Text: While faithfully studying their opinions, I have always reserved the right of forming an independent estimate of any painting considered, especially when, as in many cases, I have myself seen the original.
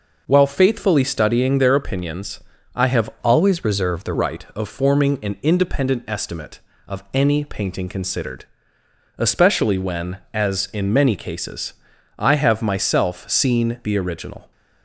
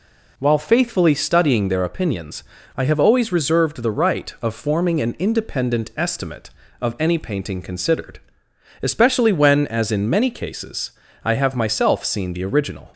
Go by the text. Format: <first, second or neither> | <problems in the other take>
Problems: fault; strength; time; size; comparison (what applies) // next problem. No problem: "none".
second | changes voice from "always" to "the"; from 3.1 to 4.1 s; 1.0 s long